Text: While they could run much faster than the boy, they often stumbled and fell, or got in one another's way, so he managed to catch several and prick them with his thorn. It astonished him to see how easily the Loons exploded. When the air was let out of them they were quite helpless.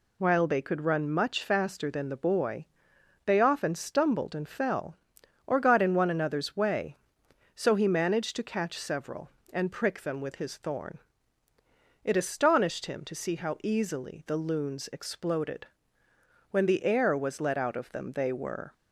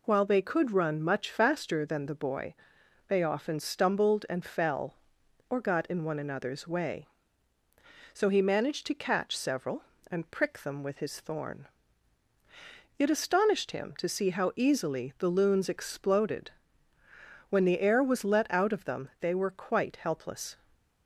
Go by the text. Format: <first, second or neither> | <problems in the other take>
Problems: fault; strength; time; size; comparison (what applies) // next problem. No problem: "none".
second | stops before "quite helpless"; at 18.7 s